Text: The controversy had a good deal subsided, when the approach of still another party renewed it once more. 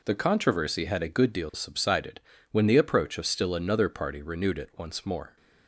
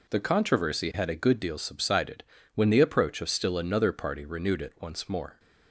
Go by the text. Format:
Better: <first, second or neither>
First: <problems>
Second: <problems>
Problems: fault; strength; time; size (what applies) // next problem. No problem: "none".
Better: neither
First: none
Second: none